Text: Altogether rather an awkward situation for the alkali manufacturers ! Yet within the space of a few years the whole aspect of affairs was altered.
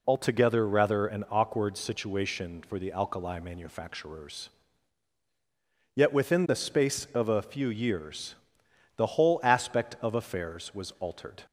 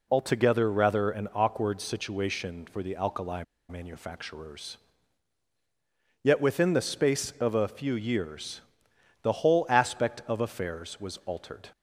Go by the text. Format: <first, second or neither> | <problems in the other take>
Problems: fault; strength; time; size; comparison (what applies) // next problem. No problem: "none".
first | pauses between "alkali" and "manufacturers"; slight; at 3.4 s; 0.26 s long // pauses between "years" and "the"; noticeable; at 8.6 s; 0.58 s long; noticeable in the first